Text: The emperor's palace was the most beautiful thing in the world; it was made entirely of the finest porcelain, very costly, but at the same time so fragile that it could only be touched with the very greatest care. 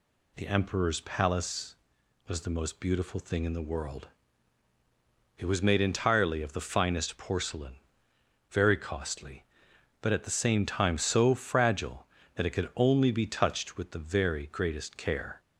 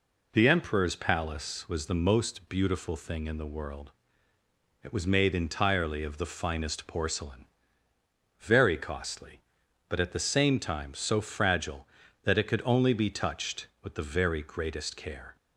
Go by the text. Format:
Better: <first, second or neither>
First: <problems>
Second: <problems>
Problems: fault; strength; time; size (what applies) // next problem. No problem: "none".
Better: neither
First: none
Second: none